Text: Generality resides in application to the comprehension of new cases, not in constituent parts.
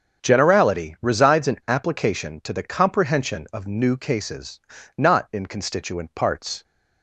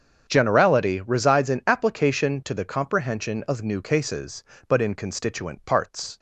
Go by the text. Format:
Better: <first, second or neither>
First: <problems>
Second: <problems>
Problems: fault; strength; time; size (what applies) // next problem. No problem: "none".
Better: first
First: starts louder than the rest; strong; until 1.2 s; 7.5 dB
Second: starts louder than the rest; strong; until 1.2 s; 7.5 dB // says "but" for "not"; at 4.6 s